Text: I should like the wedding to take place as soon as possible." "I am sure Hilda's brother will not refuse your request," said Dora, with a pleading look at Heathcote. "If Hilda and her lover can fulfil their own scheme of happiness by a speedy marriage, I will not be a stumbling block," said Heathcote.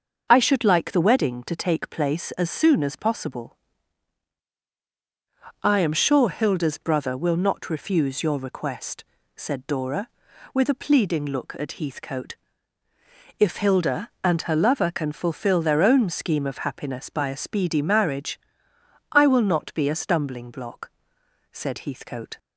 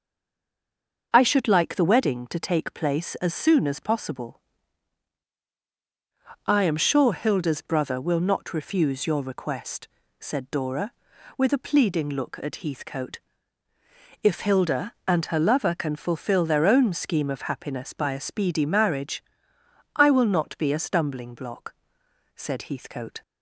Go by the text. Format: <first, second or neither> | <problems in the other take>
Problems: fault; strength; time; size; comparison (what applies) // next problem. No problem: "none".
first | stays silent before the first word; until 1.1 s; 1.1 s long // starts louder than the rest; until 2.1 s; 6.5 dB; also in the first